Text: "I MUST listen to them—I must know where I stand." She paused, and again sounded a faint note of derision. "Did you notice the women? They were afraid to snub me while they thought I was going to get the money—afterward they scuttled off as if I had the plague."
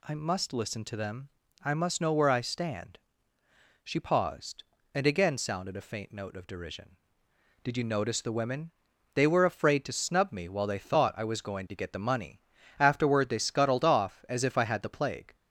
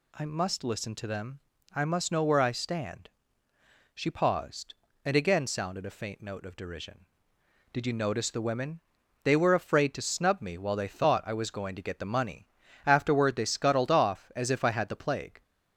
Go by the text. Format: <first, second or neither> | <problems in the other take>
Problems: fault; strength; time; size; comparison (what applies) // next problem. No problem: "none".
neither | none